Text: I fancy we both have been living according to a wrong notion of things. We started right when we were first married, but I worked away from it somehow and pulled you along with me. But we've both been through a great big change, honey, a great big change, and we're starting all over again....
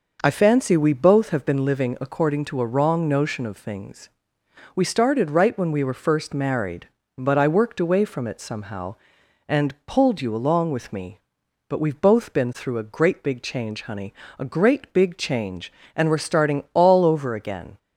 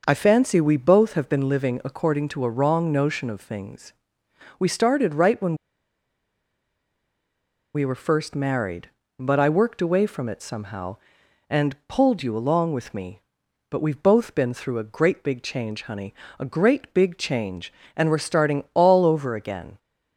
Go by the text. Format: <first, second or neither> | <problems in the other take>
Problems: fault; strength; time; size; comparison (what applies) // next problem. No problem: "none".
first | pauses between "when" and "we"; strong; at 5.5 s; 2.2 s long